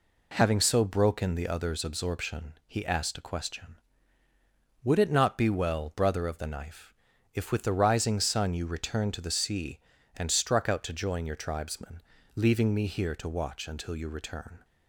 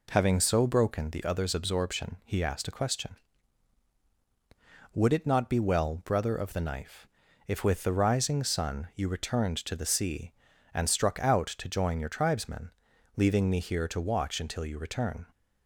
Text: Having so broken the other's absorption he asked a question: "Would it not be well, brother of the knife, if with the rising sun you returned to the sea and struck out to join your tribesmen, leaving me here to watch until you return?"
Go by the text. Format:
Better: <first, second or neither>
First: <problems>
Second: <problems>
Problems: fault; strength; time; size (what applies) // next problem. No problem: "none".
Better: neither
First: none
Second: none